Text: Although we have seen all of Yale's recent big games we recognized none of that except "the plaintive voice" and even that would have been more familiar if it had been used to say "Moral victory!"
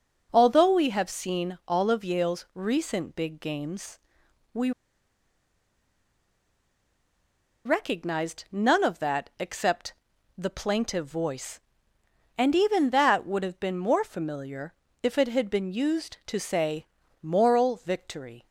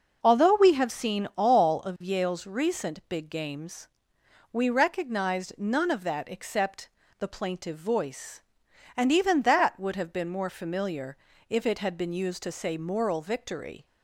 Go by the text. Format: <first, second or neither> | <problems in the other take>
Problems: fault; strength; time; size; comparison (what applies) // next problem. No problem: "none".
second | pauses between "games" and "we"; noticeable; at 3.9 s; 0.54 s long; noticeable in the second // pauses between "we" and "recognized"; strong; at 4.7 s; 2.9 s long // pauses between "except" and "the"; noticeable; at 9.9 s; 0.46 s long; slight in the second // pauses between "familiar" and "if"; slight; at 14.7 s; 0.30 s long; slight in the second // pauses between "say" and "Moral"; slight; at 16.8 s; 0.34 s long